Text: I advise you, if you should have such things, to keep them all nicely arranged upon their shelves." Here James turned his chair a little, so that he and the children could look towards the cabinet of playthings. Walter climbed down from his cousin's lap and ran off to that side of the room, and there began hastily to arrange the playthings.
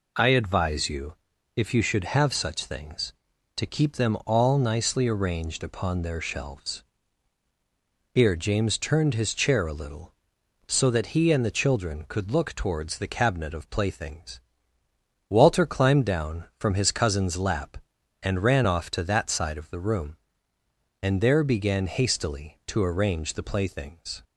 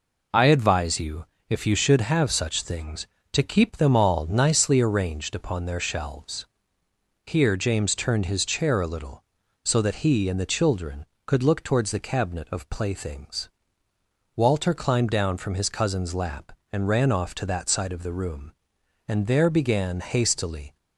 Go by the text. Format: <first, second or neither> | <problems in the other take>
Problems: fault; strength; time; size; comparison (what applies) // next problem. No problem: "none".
first | stops before "to arrange the playthings"; at 20.7 s